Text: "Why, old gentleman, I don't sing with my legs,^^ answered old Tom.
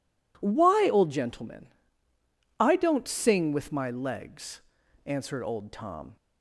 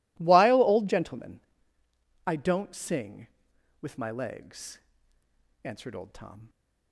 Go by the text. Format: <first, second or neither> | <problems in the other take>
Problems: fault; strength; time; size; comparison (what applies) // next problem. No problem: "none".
first | says "While" for "Why"; at 0.1 s